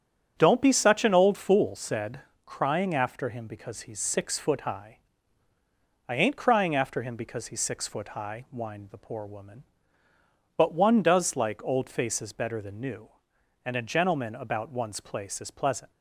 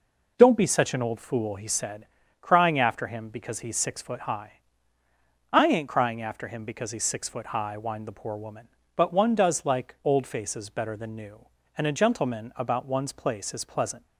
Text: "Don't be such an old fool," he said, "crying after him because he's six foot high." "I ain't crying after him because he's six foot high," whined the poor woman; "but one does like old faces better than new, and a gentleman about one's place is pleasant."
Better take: second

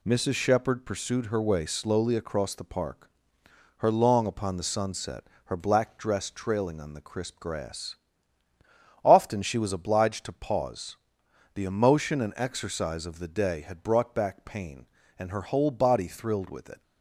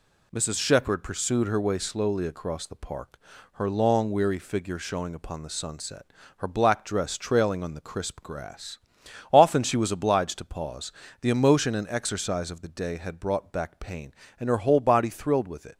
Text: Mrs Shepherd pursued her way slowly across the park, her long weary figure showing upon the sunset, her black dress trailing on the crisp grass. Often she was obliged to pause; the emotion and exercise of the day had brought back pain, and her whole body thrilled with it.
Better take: second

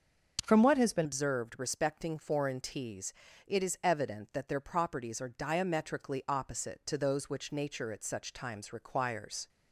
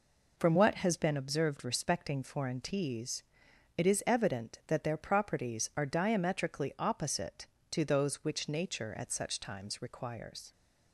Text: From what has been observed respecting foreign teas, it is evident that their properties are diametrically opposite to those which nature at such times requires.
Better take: second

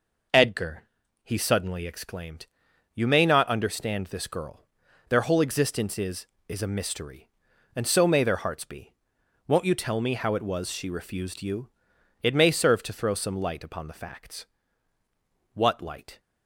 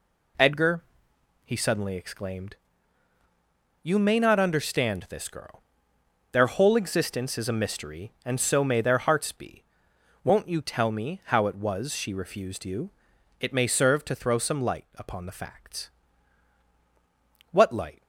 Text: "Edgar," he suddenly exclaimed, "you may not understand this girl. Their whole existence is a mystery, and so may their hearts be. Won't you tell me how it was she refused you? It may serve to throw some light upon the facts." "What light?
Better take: second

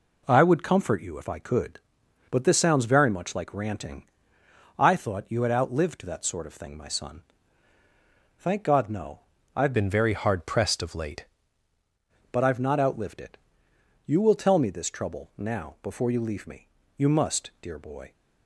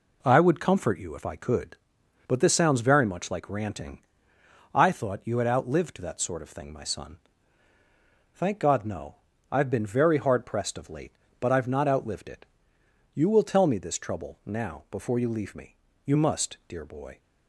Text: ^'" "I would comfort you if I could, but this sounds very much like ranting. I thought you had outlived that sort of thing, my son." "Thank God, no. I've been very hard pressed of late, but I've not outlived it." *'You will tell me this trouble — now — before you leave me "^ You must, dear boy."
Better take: second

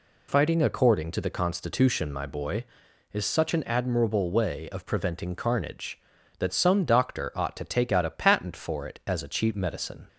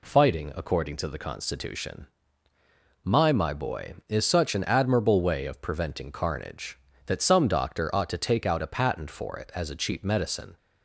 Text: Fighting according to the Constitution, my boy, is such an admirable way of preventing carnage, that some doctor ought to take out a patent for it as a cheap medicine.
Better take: first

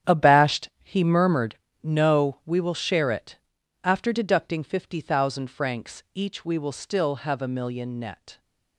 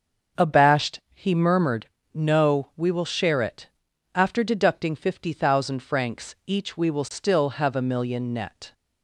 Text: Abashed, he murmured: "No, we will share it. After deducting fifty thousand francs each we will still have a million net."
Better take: second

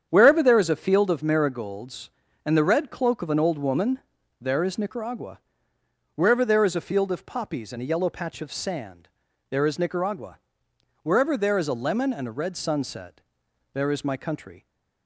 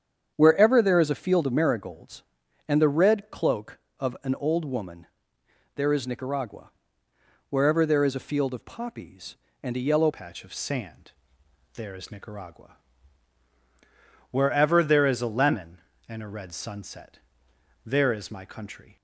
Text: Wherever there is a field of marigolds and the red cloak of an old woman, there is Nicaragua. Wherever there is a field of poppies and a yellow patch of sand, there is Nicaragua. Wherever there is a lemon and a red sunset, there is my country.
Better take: first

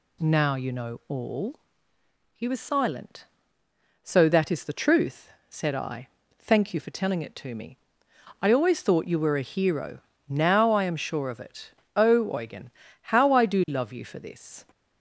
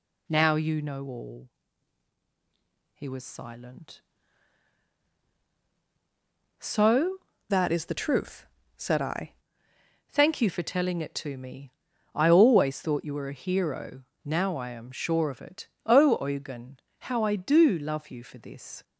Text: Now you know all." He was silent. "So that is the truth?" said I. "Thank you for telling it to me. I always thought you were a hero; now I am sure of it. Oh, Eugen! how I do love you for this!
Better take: first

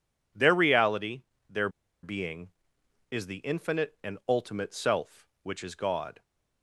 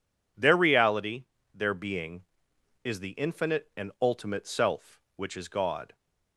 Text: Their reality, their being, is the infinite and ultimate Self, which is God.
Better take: second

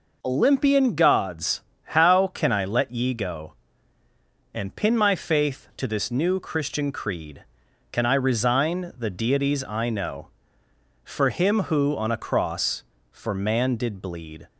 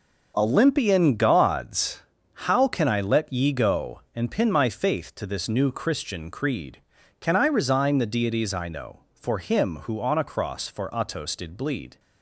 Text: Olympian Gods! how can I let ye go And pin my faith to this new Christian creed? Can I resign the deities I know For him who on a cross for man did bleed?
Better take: first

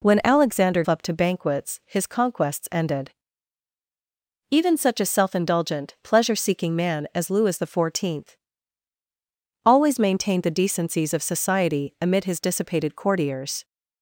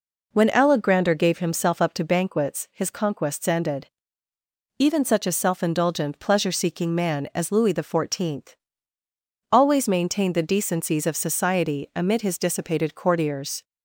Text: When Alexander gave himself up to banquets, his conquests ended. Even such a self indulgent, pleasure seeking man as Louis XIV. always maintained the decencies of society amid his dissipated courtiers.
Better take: second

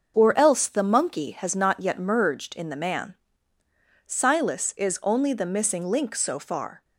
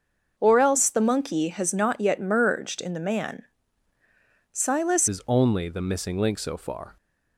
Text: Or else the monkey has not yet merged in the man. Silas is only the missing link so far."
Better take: first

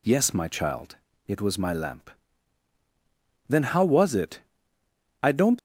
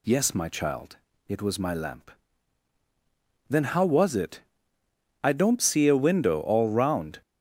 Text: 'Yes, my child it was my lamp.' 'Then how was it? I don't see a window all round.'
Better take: second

